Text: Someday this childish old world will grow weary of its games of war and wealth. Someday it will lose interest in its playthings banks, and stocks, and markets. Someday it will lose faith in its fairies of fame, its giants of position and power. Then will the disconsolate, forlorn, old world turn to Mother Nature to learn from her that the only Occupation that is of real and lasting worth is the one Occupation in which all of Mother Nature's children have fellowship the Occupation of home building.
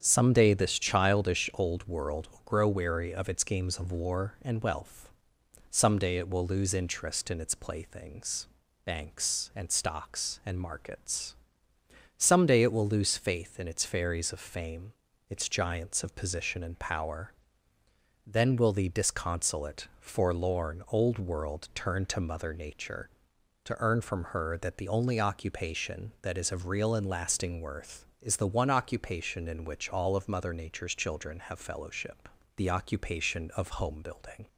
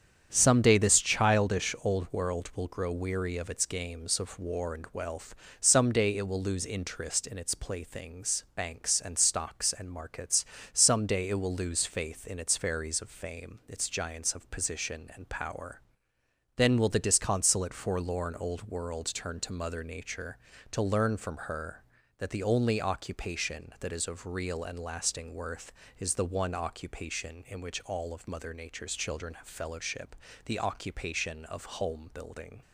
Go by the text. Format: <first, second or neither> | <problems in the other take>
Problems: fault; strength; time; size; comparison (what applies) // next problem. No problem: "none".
second | starts louder than the rest; strong; until 1.0 s; 8 dB; strong in the second // pauses between "playthings" and "banks"; slight; at 8.4 s; 0.36 s long // says "earn" for "learn"; at 23.7 s // pauses between "fellowship" and "the"; slight; at 32.2 s; 0.28 s long; slight in the second